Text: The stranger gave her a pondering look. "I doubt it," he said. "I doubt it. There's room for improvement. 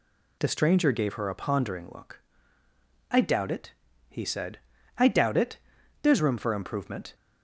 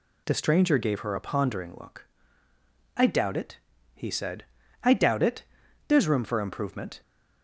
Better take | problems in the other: neither | none

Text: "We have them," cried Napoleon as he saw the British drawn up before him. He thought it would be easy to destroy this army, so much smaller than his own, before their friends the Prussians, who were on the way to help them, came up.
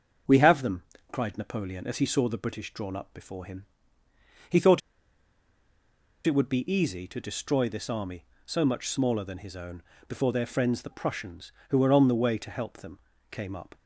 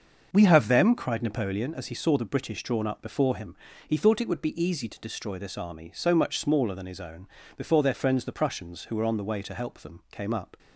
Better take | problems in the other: second | starts louder than the rest; until 1.5 s; 6.5 dB; also in the second // pauses between "thought" and "it"; strong; at 4.8 s; 1.4 s long

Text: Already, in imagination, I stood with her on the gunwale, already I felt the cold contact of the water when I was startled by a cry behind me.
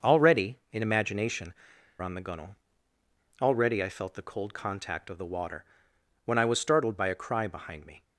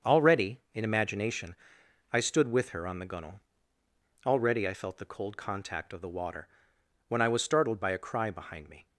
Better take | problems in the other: second | starts louder than the rest; until 1.1 s; 6 dB; also in the second // skips "I stood with her"; at 1.7 s // pauses between "water" and "when"; noticeable; at 5.6 s; 0.60 s long; noticeable in the second

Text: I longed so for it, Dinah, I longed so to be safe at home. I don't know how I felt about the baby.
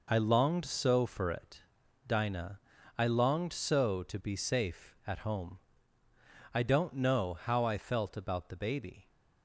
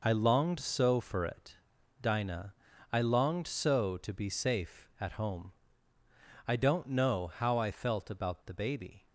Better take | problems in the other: neither | none

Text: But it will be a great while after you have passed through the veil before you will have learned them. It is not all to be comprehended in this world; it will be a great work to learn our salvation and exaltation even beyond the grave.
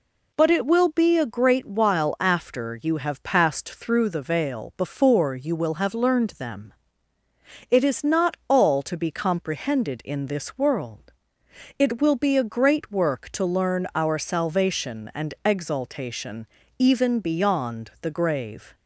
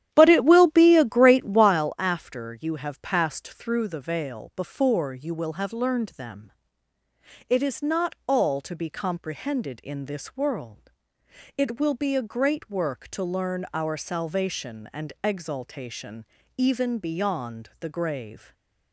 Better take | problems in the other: first | starts louder than the rest; strong; until 1.9 s; 11 dB // pauses between "exaltation" and "even"; slight; at 16.2 s; 0.32 s long; slight in the first // stays silent after the last word; slight; from 18.3 s on; 0.6 s long

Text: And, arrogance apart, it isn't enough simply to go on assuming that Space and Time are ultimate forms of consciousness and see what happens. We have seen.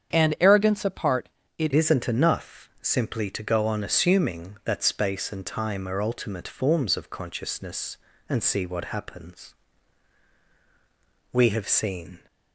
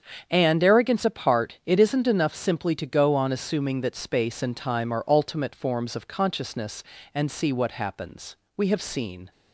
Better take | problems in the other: second | starts louder than the rest; strong; until 1.2 s; 8 dB; strong in the second // changes voice at "isn't"; from 1.7 s on; 10.4 s long

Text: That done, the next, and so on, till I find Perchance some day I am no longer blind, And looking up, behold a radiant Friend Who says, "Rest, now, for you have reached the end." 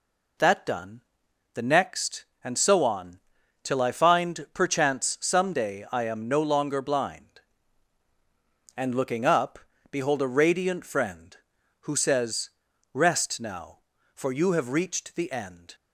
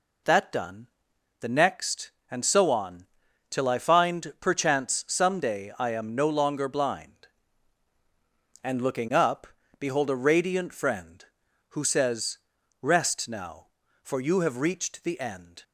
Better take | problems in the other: neither | none

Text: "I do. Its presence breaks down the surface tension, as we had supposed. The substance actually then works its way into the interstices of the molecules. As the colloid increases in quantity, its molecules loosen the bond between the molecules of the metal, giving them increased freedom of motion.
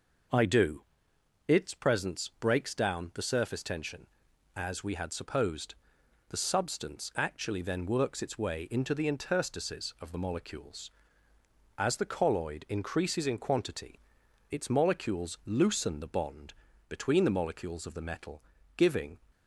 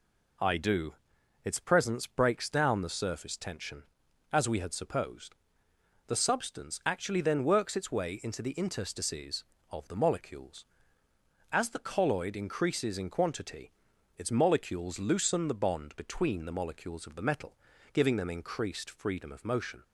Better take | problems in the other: second | pauses between "bond" and "between"; at 16.5 s; 0.38 s long // stops before "them increased freedom of motion"; at 19.3 s

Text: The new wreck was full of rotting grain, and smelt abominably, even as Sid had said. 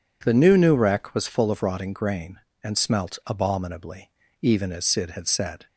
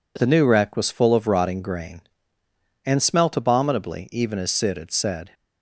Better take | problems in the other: second | says "new" twice; at 0.5 s

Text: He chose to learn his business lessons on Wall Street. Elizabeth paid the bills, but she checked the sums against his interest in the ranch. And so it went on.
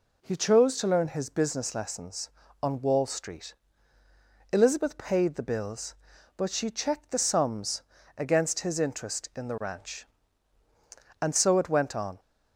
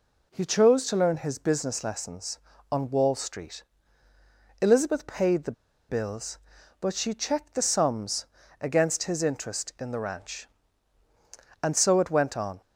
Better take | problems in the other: first | pauses between "the" and "bills"; at 5.5 s; 0.36 s long // pauses between "sums" and "against"; slight; at 8.2 s; 0.36 s long; slight in the first

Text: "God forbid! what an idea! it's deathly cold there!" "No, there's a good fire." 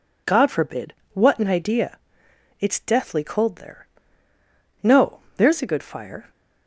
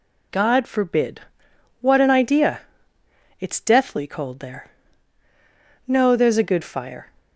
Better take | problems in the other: neither | none

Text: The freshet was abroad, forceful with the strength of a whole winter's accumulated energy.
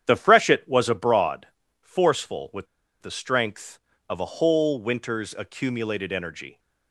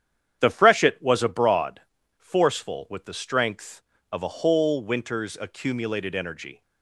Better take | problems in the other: second | starts louder than the rest; strong; until 1.0 s; 9 dB; strong in the second // pauses between "with" and "the"; at 2.6 s; 0.36 s long

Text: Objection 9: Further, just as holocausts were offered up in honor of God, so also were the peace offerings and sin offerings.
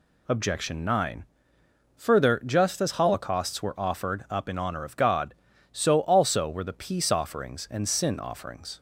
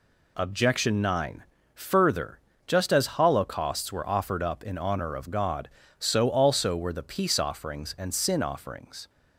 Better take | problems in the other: neither | none

